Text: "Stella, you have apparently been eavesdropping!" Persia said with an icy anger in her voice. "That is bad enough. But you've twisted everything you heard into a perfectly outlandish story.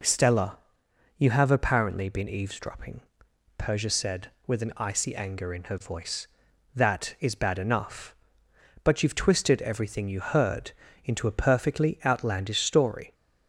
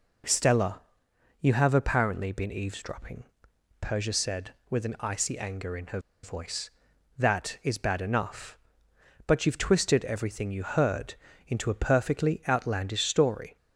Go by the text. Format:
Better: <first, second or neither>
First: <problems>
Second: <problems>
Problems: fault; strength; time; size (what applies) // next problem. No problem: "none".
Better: first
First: pauses between "heard" and "into"; slight; at 10.7 s; 0.34 s long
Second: pauses between "her" and "voice"; slight; at 5.9 s; 0.24 s long // pauses between "heard" and "into"; slight; at 11.1 s; 0.34 s long